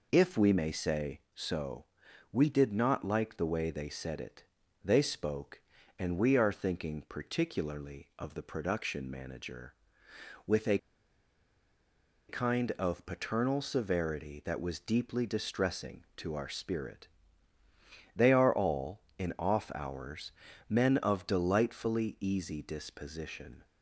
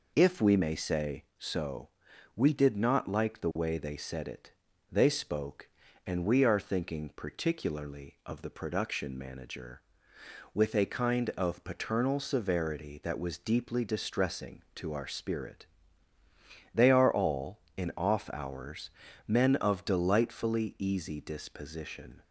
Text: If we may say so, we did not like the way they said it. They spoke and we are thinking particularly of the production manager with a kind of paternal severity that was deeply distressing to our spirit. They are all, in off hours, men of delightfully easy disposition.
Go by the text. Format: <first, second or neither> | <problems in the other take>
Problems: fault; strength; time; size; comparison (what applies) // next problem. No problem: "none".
second | pauses between "a" and "kind"; strong; at 10.7 s; 1.5 s long